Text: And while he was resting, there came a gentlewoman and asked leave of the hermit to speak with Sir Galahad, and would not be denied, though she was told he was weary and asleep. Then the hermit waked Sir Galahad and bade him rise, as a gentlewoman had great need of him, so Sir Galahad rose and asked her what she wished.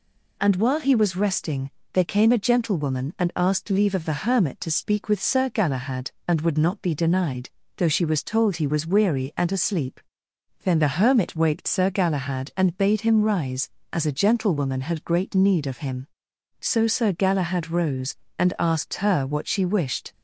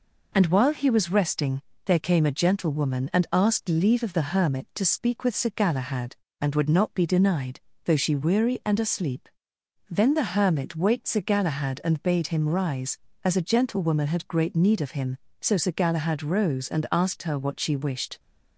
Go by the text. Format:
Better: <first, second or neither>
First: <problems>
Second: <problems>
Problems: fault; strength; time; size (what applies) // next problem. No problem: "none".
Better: first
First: none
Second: skips "was told he was"; at 8.1 s